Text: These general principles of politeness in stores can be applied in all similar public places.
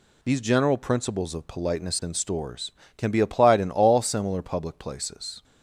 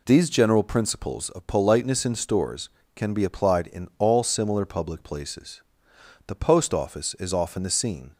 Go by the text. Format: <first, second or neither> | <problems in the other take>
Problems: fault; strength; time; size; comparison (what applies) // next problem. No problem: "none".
first | goes on to say "The post office is often the scene"; strong; from 6.2 s on; 1.8 s long